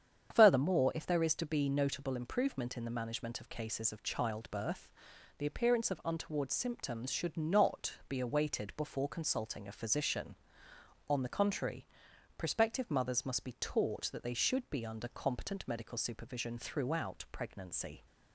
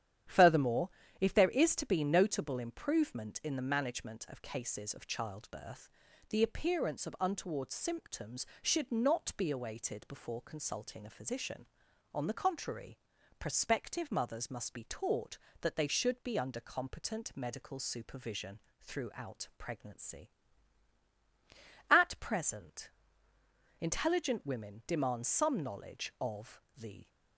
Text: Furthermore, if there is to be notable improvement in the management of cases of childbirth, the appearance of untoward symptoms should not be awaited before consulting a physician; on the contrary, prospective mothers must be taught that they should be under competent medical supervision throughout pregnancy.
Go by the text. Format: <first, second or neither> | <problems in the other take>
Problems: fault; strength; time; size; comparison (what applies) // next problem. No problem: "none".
first | starts louder than the rest; strong; until 1.5 s; 10 dB; strong in the first // pauses between "supervision" and "throughout"; slight; at 18.6 s; 0.20 s long // goes on to say "At present intelligent women demand some knowledge of the"; strong; from 21.9 s on; 5.1 s long